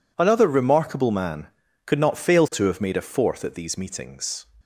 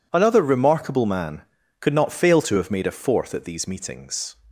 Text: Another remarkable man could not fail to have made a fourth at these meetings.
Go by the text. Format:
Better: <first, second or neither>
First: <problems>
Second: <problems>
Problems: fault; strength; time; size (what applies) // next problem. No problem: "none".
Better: neither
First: none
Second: none